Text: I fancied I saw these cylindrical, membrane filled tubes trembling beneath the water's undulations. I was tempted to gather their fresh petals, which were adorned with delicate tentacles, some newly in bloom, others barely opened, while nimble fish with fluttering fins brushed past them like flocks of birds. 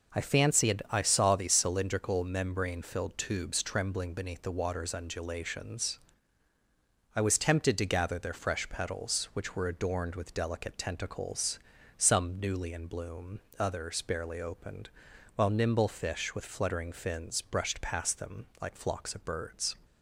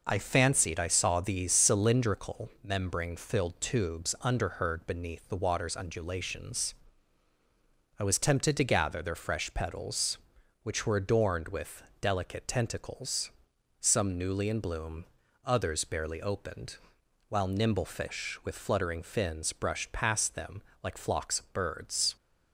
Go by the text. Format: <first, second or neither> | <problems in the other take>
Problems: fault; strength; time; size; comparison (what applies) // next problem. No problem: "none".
first | says "underheard" for "trembling"; at 4.2 s // pauses between "with" and "delicate"; slight; at 11.8 s; 0.18 s long // pauses between "them" and "like"; slight; at 20.6 s; 0.18 s long